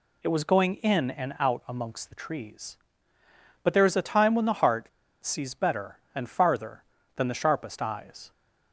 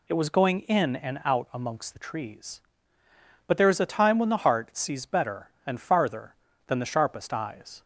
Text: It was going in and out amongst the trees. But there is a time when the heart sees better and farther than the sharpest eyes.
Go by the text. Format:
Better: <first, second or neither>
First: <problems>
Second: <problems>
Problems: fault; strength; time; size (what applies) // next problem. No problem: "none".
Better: second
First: pauses between "heart" and "sees"; slight; at 4.8 s; 0.33 s long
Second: none